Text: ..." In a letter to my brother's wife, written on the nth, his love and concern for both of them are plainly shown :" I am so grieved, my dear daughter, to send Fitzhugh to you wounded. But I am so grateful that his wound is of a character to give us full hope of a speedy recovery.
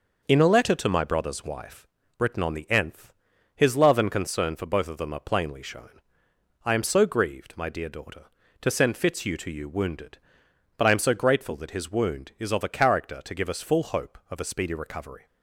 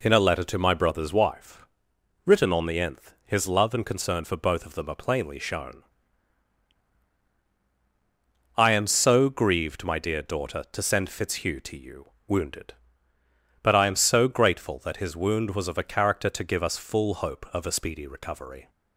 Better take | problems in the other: first | pauses between "you" and "wounded"; slight; at 12.0 s; 0.16 s long // says "was" for "is"; at 15.5 s

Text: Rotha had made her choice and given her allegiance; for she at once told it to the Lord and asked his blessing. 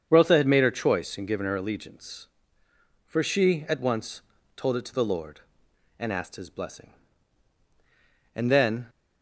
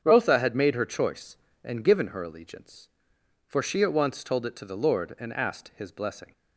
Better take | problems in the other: second | starts louder than the rest; strong; until 1.1 s; 7.5 dB; strong in the second // pauses between "once" and "told"; slight; at 4.2 s; 0.34 s long // goes on to say "And then"; from 8.3 s on; 0.54 s long

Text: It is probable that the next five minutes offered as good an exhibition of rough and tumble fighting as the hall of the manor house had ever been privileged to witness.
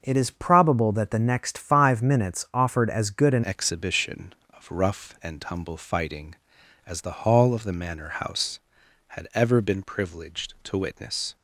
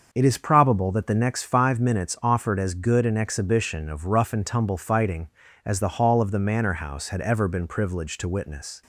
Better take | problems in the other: second | starts louder than the rest; until 1.0 s; 6.5 dB; also in the second // changes voice at "exhibition"; from 3.4 s on; 7.9 s long

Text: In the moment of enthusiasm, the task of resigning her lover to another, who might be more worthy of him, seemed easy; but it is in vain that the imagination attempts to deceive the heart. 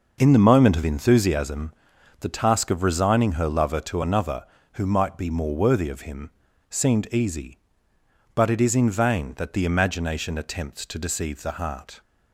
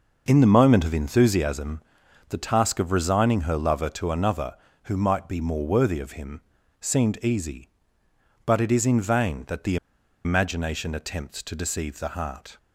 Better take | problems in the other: first | pauses between "the" and "imagination"; noticeable; at 9.7 s; 0.47 s long

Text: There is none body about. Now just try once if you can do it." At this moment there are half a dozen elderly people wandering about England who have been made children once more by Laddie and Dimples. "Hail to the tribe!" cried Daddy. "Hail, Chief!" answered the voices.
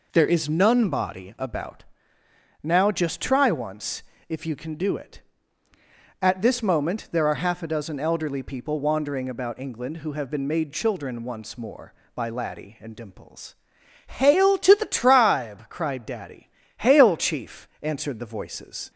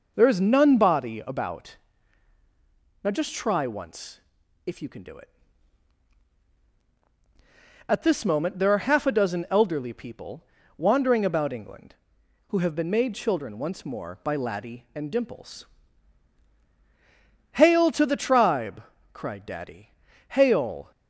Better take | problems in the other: first | pauses between "once" and "if"; at 4.2 s; 0.44 s long; slight in the first // pauses between "people" and "wandering"; slight; at 10.4 s; 0.34 s long // stops before "Chief answered the voices"; at 20.9 s

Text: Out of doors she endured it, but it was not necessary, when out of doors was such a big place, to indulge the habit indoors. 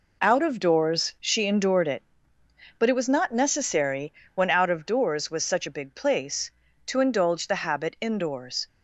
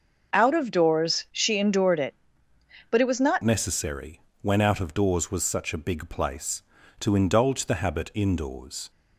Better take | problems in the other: first | starts louder than the rest; noticeable; until 1.3 s; 6 dB // changes voice at "necessary"; from 3.4 s on; 5.5 s long

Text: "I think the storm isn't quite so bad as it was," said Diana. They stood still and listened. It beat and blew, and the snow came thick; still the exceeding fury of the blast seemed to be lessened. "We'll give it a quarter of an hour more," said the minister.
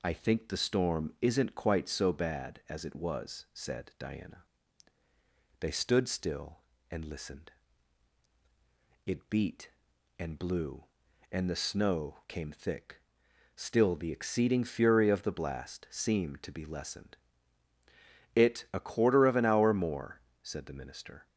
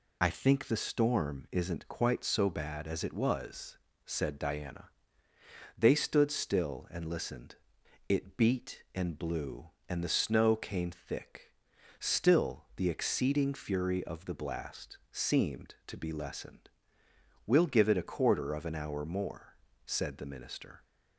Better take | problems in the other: second | skips "We'll give"; at 17.7 s

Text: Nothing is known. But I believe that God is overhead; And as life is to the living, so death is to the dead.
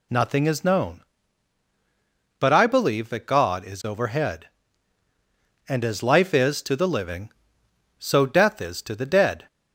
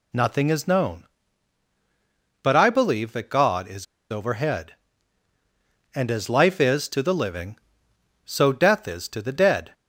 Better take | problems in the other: first | pauses between "is" and "overhead"; slight; at 3.8 s; 0.26 s long

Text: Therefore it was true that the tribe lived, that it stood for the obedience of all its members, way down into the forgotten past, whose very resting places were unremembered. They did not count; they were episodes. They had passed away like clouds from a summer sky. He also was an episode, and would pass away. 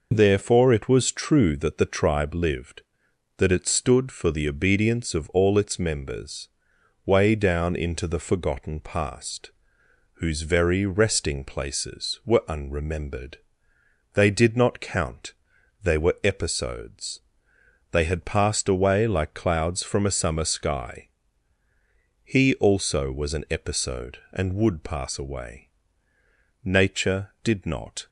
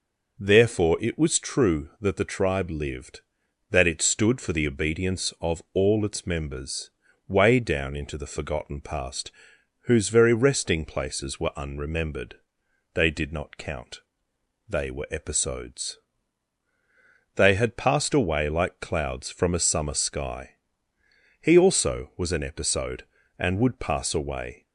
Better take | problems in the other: second | goes on to say "Nature did not"; from 26.6 s on; 1.4 s long

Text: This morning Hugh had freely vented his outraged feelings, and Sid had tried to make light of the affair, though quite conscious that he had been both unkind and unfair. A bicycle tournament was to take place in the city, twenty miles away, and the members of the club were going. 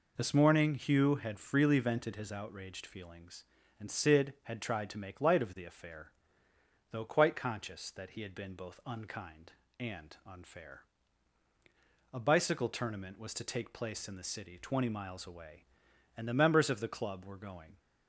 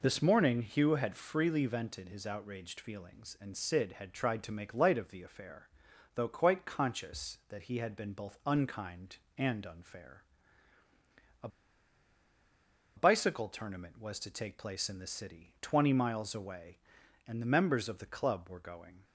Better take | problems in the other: first | pauses between "A" and "bicycle"; strong; at 11.4 s; 1.4 s long

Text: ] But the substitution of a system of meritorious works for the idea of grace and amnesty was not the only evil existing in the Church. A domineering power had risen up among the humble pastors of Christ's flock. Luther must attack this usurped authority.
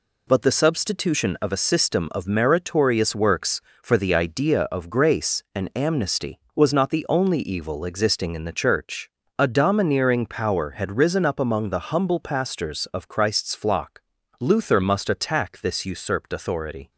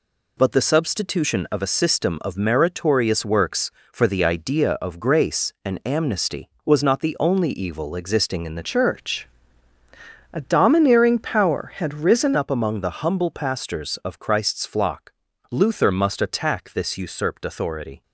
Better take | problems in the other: first | changes voice from "Church" to "risen"; from 8.6 to 12.3 s; 3.7 s long

